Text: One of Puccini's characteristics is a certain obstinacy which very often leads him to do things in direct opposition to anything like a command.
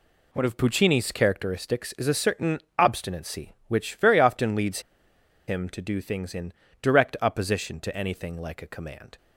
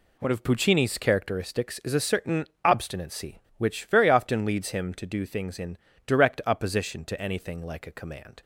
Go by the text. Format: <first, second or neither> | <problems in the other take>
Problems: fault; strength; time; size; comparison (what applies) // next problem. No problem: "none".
second | pauses between "certain" and "obstinacy"; slight; at 2.5 s; 0.18 s long; slight in the second // pauses between "leads" and "him"; noticeable; at 4.7 s; 0.68 s long // pauses between "in" and "direct"; slight; at 6.5 s; 0.28 s long; slight in the second